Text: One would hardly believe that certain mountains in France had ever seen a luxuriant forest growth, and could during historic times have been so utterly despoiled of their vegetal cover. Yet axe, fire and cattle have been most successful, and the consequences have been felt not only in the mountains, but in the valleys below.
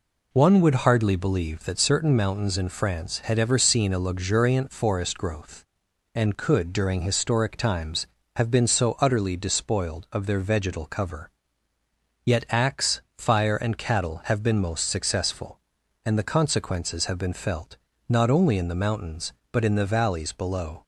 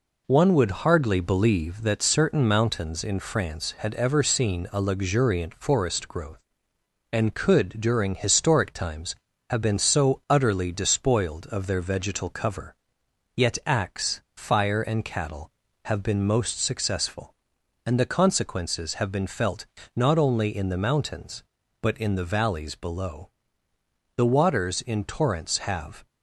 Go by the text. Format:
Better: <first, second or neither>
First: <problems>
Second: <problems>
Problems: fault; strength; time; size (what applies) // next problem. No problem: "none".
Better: first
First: pauses between "felt" and "not"; slight; at 17.7 s; 0.32 s long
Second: pauses between "felt" and "not"; slight; at 19.6 s; 0.28 s long // goes on to say "The waters in torrents have"; strong; from 24.1 s on; 1.9 s long